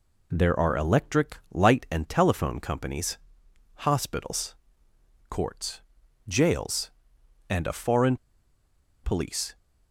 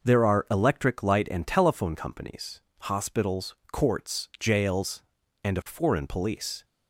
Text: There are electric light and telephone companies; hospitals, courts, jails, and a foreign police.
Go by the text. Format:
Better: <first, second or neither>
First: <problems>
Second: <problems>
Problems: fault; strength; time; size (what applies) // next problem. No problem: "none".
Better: second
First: pauses between "foreign" and "police"; noticeable; at 8.1 s; 0.88 s long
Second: none